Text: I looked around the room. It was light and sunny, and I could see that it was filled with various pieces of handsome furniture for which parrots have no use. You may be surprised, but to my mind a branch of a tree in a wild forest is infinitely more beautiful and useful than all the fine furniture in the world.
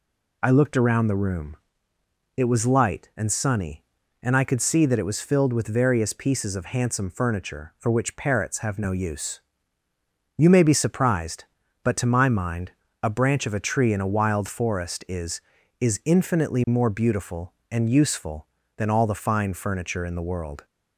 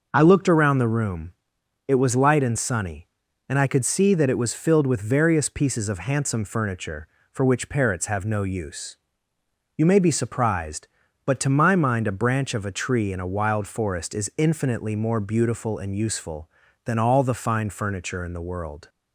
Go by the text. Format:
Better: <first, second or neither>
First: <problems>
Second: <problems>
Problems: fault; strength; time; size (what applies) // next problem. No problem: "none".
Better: second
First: pauses between "mind" and "a"; slight; at 12.7 s; 0.30 s long // says "is" twice; at 15.7 s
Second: none